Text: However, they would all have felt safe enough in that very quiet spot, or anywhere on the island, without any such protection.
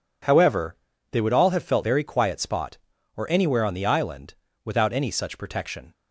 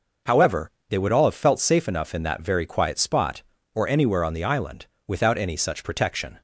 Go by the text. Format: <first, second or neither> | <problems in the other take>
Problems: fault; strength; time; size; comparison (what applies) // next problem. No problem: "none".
second | skips "safe enough in that"; at 1.8 s